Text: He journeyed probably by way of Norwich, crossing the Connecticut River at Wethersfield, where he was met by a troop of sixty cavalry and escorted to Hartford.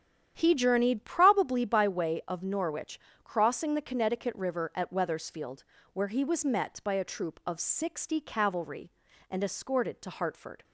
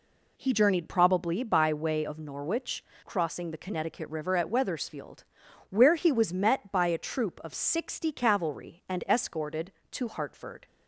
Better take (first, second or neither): second